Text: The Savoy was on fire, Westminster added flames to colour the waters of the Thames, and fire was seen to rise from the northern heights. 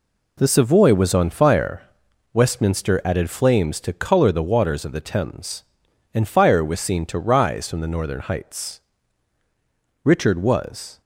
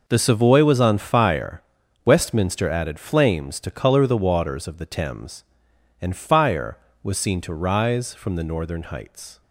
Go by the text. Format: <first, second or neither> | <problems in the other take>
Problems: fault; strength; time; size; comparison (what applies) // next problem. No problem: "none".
second | goes on to say "Richard was"; noticeable; from 10.0 s on; 0.96 s long